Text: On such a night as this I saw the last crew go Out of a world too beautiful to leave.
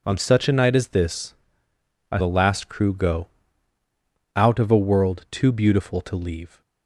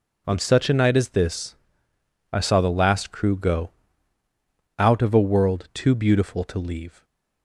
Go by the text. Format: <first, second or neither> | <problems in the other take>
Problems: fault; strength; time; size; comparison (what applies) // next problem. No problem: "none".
second | pauses between "this" and "I"; noticeable; at 1.3 s; 0.76 s long; noticeable in the second // skips "saw"; at 2.1 s // pauses between "go" and "Out"; at 3.2 s; 1.0 s long; also in the second